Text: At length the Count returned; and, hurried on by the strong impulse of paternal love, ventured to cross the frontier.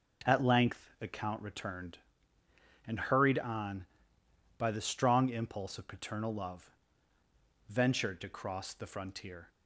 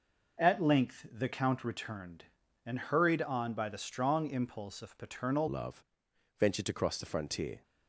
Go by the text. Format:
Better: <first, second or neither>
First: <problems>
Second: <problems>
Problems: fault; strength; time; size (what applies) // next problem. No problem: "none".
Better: first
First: none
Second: changes voice at "love"; from 5.4 s on; 2.2 s long